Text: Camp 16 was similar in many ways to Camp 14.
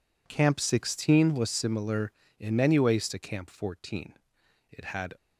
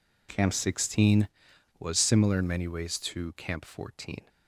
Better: second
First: goes on to say "It had"; slight; from 4.6 s on; 0.46 s long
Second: none

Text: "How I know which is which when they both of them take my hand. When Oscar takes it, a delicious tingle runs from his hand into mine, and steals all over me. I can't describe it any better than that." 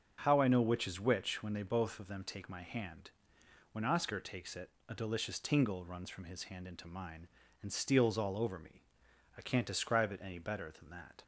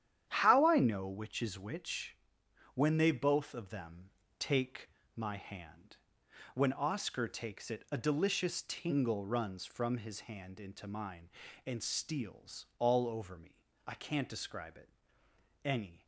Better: first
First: none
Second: starts louder than the rest; strong; until 1.3 s; 10 dB // pauses between "which" and "when"; noticeable; at 2.1 s; 0.58 s long // pauses between "them" and "take"; slight; at 4.0 s; 0.28 s long // pauses between "take" and "my"; slight; at 4.8 s; 0.26 s long // pauses between "it" and "any"; noticeable; at 14.8 s; 0.76 s long // stops before "better than that"; at 16.0 s

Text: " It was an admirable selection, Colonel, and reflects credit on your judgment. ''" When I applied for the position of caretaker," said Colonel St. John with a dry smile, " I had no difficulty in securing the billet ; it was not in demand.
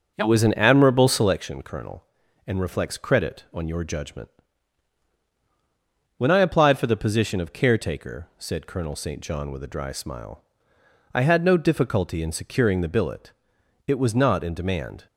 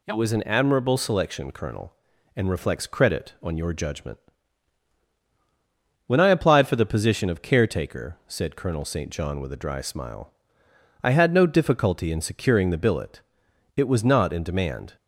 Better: second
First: starts louder than the rest; until 1.4 s; 7 dB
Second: none

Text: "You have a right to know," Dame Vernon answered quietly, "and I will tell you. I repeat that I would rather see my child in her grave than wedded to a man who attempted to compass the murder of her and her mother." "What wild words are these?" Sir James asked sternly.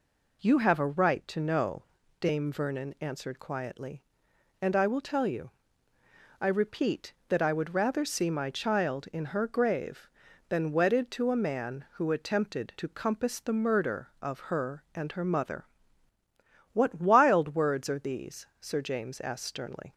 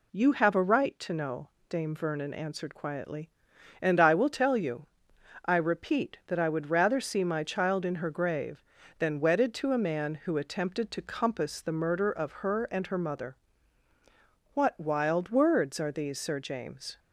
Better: first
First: none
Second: stops before "asked sternly"; at 16.9 s

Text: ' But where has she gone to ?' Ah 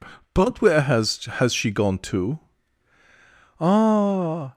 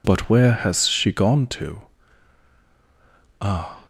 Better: second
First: says "has" twice; at 1.2 s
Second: none

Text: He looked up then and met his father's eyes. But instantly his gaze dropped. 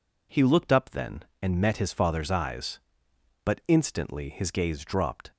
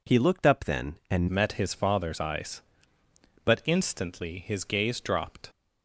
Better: first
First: none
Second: changes voice at "met"; from 1.2 s on; 4.2 s long

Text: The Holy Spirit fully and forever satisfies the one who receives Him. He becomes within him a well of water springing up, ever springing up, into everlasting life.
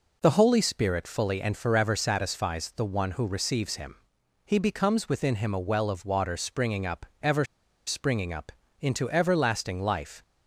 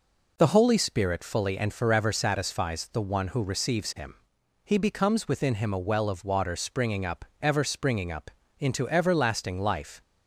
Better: second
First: pauses between "ever" and "springing"; at 7.4 s; 0.43 s long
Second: none

